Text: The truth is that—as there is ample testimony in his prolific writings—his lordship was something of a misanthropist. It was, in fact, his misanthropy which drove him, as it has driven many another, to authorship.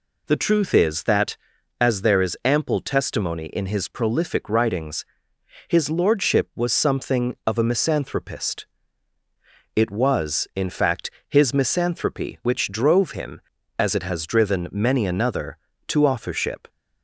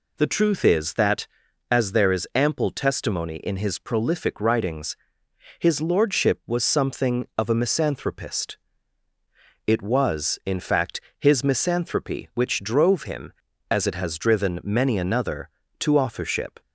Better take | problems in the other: neither | none

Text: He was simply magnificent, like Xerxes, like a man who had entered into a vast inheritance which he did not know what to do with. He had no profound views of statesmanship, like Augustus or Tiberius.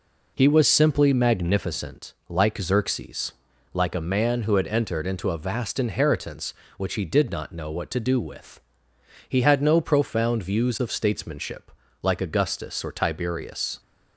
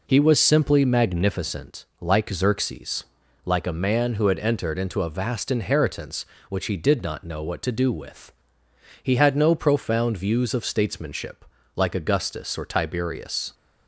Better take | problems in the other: neither | none

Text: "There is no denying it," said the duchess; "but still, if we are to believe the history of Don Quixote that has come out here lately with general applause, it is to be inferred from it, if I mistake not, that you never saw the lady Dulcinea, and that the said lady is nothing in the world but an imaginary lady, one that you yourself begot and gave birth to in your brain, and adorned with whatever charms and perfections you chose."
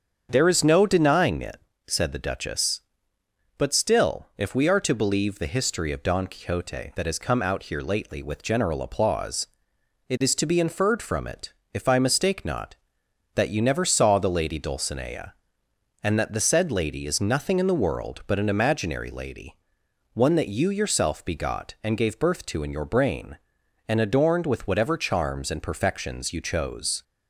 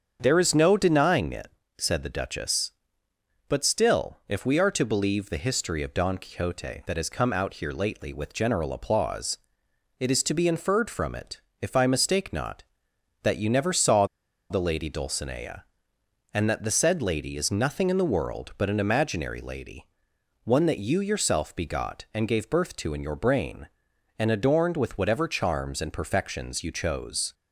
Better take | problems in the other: first | starts louder than the rest; strong; until 1.2 s; 7.5 dB; strong in the first // pauses between "saw" and "the"; at 14.0 s; 0.45 s long

